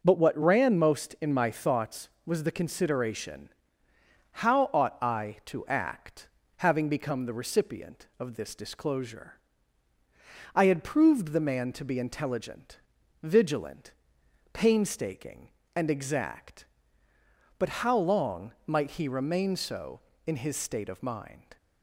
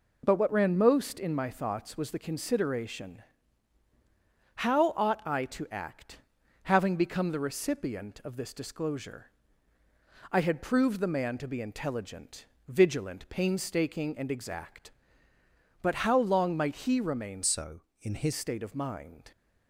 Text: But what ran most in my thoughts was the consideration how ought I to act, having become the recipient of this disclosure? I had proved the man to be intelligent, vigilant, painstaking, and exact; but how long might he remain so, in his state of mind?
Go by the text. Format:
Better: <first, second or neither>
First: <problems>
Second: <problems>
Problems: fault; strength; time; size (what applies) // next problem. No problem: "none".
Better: first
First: pauses between "consideration" and "how"; noticeable; at 3.4 s; 0.92 s long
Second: pauses between "consideration" and "how"; strong; at 3.2 s; 1.3 s long // changes voice from "so" to "his"; from 17.4 to 18.3 s; 0.9 s long